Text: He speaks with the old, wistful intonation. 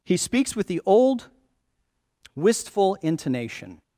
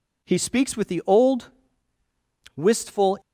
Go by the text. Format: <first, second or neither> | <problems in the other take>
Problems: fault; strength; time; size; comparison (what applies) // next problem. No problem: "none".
first | stops before "intonation"; at 3.2 s